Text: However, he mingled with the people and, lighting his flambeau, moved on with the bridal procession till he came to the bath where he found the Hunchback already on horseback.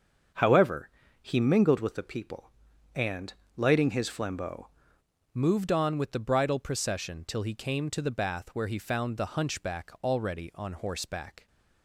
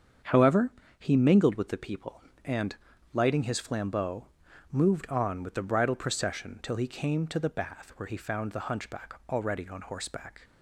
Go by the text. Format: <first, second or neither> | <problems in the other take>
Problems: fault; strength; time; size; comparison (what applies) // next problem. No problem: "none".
second | starts louder than the rest; until 1.6 s; 6.5 dB; strong in the second // changes voice at "moved"; from 5.3 s on; 6.1 s long